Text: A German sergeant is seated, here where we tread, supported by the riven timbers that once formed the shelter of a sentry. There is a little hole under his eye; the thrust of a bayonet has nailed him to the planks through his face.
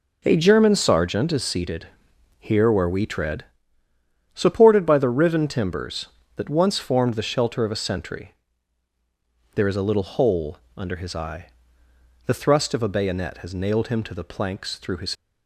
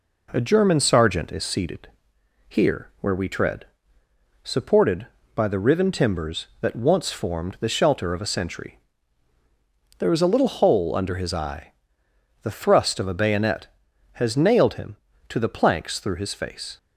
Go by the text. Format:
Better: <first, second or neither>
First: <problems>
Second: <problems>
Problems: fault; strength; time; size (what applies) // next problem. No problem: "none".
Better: second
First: pauses between "hole" and "under"; slight; at 10.5 s; 0.18 s long // stops before "face"; at 15.1 s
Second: none